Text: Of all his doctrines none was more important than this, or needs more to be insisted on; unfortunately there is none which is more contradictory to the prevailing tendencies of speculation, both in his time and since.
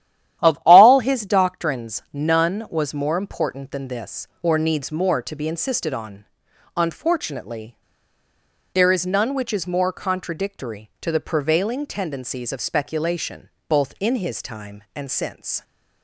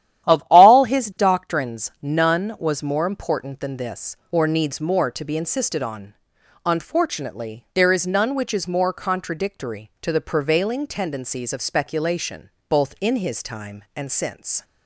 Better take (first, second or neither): second